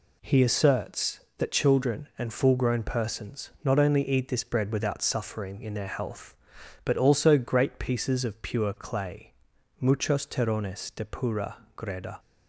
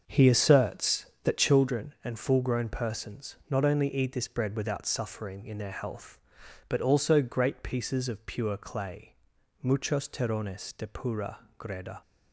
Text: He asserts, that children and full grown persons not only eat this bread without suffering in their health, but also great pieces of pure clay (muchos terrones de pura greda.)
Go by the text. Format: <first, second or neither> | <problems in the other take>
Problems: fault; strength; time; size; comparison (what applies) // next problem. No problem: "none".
first | starts louder than the rest; until 1.8 s; 6.5 dB // pauses between "pura" and "greda"; slight; at 11.3 s; 0.18 s long; slight in the first